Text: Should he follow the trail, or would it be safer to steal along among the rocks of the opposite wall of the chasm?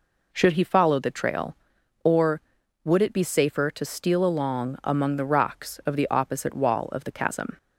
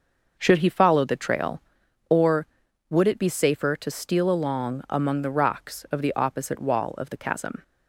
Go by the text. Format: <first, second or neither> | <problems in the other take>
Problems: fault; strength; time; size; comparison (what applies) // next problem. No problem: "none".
first | gets quieter; strong; throughout; 8.5 dB